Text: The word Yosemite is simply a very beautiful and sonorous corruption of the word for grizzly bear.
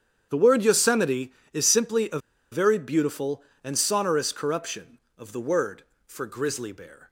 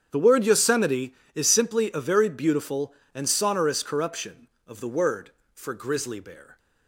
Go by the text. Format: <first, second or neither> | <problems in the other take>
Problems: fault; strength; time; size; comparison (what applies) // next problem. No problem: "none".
second | starts louder than the rest; strong; until 1.3 s; 8.5 dB; strong in the second // pauses between "a" and "very"; slight; at 2.1 s; 0.33 s long